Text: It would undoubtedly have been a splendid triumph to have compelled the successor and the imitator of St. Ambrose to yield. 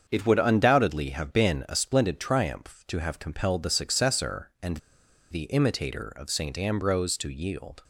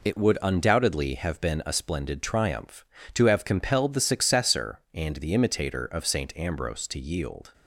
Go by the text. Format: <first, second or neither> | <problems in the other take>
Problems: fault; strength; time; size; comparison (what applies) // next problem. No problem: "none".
second | starts louder than the rest; until 1.0 s; 7 dB // pauses between "and" and "the"; noticeable; at 4.7 s; 0.53 s long